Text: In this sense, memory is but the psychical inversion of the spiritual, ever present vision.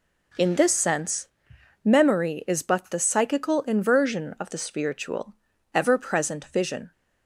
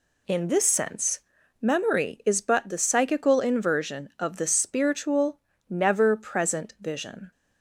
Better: first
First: none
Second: says "never" for "ever"; at 5.6 s

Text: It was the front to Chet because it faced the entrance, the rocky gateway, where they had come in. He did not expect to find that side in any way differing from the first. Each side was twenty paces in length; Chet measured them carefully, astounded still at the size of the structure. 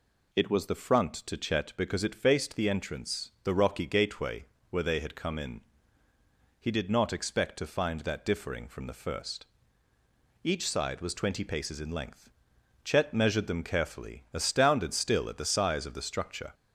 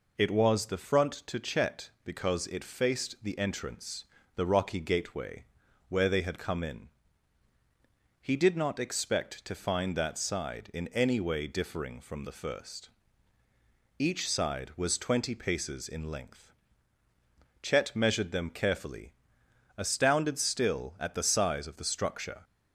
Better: second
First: skips "side in any way"; at 8.2 s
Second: none

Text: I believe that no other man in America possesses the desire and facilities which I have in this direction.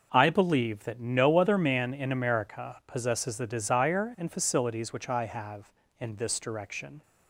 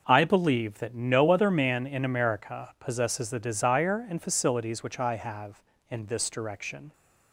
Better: neither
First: none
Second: none

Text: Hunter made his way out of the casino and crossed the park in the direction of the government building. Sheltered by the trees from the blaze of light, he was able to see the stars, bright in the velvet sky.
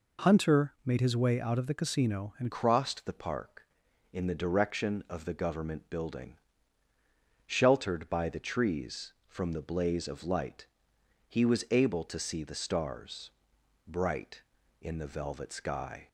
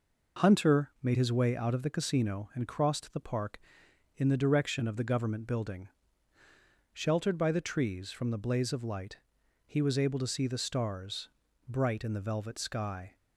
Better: second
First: changes voice at "crossed"; from 2.5 s on; 13.5 s long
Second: none

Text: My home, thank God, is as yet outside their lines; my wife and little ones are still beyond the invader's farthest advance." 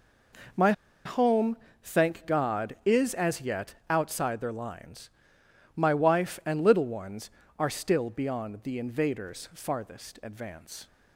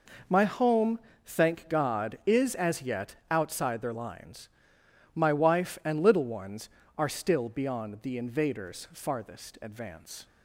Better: second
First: pauses between "My" and "home"; slight; at 0.7 s; 0.33 s long // pauses between "yet" and "outside"; slight; at 3.7 s; 0.16 s long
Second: pauses between "yet" and "outside"; slight; at 3.1 s; 0.16 s long

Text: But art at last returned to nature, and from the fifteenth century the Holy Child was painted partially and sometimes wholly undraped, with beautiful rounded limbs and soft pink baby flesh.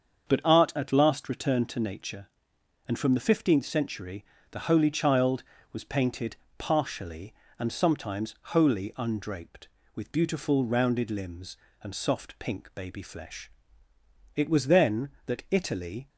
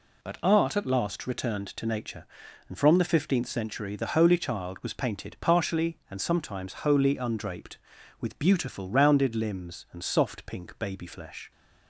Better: second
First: starts louder than the rest; until 1.3 s; 7 dB // pauses between "century" and "the"; slight; at 4.2 s; 0.28 s long // pauses between "painted" and "partially"; slight; at 6.3 s; 0.23 s long // goes on to say "It was then that Italy"; strong; from 14.3 s on; 1.7 s long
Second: none

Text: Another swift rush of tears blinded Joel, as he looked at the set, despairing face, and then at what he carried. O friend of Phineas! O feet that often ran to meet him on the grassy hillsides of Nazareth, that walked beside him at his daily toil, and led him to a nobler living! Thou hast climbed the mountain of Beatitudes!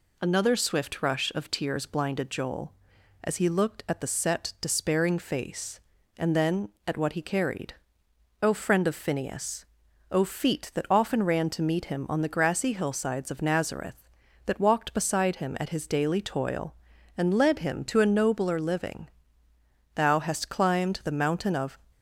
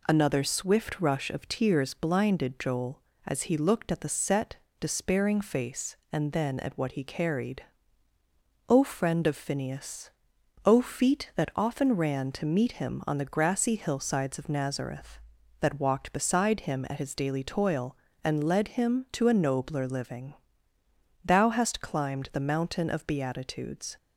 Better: second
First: stops before "Beatitudes"; at 21.9 s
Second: none

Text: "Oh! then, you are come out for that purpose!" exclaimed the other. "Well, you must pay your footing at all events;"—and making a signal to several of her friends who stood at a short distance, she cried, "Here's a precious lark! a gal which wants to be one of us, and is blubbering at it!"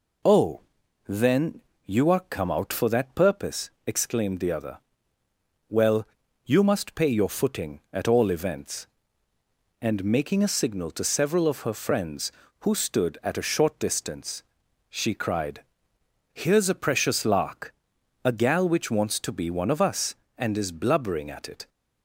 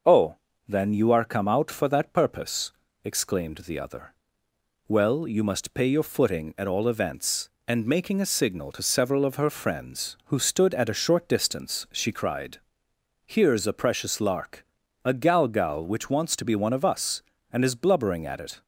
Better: first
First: none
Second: says "gal" twice; at 15.4 s

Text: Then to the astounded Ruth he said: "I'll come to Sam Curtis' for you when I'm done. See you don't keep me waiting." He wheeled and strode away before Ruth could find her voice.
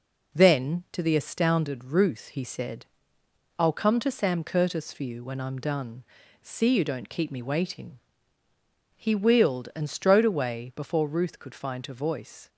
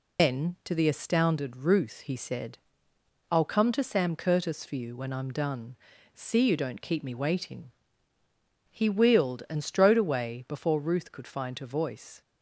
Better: first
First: none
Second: loses the start of "Then"; at 0.1 s; 135 ms

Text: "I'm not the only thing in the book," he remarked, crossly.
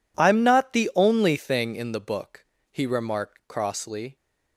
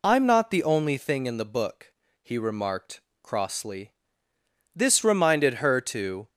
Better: first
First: none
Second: goes on to say "This reminded her to"; from 4.7 s on; 1.5 s long

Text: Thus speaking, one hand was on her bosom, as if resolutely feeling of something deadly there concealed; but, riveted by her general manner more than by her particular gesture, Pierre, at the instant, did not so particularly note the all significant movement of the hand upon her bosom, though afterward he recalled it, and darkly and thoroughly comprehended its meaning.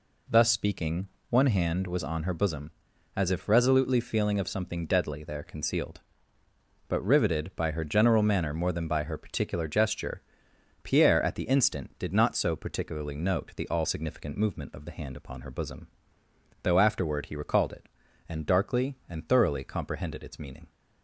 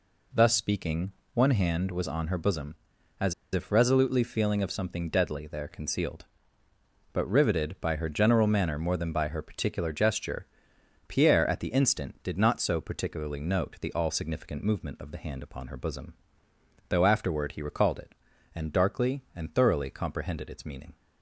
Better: first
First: none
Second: pauses between "as" and "if"; slight; at 3.3 s; 0.21 s long

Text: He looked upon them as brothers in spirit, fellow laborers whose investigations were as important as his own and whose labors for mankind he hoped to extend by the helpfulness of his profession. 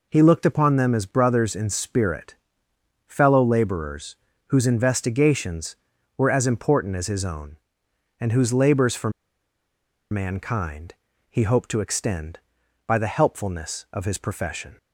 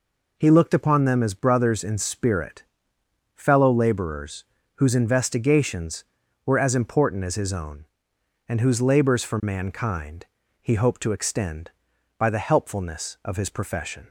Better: second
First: pauses between "laborers" and "whose"; slight; at 4.1 s; 0.30 s long // pauses between "for" and "mankind"; at 9.1 s; 1.0 s long // pauses between "mankind" and "he"; slight; at 10.9 s; 0.34 s long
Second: pauses between "laborers" and "whose"; slight; at 4.4 s; 0.30 s long // pauses between "mankind" and "he"; slight; at 10.2 s; 0.34 s long

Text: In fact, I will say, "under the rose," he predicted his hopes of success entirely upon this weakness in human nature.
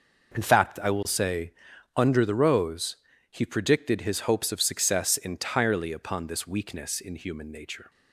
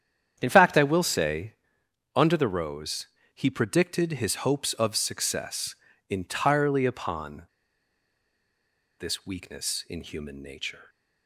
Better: first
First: none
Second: starts louder than the rest; strong; until 1.4 s; 9 dB // pauses between "success" and "entirely"; slight; at 5.7 s; 0.36 s long // pauses between "upon" and "this"; strong; at 7.4 s; 1.5 s long

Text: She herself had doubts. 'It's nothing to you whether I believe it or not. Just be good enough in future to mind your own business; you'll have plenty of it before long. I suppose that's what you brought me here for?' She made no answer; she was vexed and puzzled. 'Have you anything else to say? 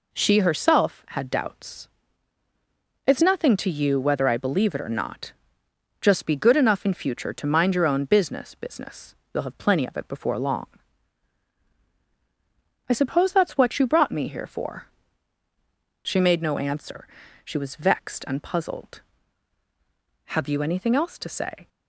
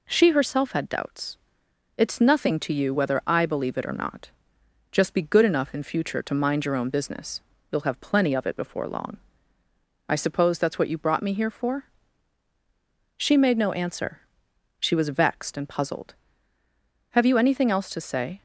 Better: second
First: says "business" twice; at 8.5 s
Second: none

